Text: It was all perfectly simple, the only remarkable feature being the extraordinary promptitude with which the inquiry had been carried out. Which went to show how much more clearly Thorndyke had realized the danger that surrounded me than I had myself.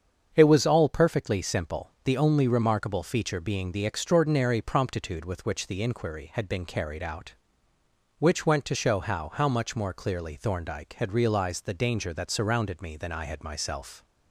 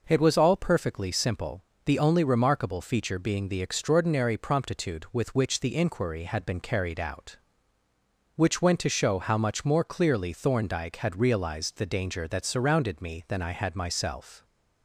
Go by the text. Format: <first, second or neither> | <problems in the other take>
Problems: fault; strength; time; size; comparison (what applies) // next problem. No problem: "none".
second | starts louder than the rest; strong; until 1.3 s; 7.5 dB // says "how" twice; at 9.3 s